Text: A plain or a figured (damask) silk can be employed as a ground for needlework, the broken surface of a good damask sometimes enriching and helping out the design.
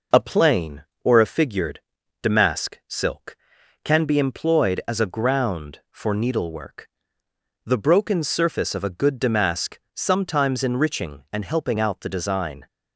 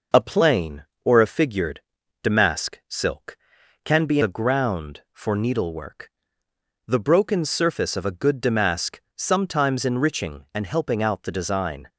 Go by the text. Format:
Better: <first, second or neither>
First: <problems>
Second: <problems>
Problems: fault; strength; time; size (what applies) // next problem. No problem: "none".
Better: first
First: pauses between "damask" and "sometimes"; slight; at 9.7 s; 0.16 s long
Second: skips "employed as"; at 4.2 s // pauses between "damask" and "sometimes"; slight; at 9.0 s; 0.16 s long